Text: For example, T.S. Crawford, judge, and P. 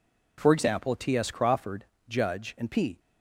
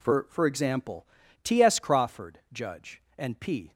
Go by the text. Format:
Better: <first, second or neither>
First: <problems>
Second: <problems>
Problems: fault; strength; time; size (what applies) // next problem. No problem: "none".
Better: first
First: none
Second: says "For" twice; at 0.2 s